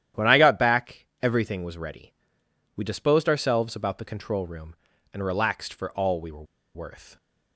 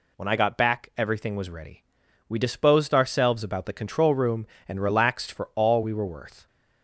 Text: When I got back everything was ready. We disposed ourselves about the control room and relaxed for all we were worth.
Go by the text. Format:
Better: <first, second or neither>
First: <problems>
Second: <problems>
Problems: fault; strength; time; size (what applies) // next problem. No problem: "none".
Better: second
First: starts louder than the rest; strong; until 1.3 s; 11 dB // pauses between "were" and "worth"; slight; at 6.4 s; 0.31 s long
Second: none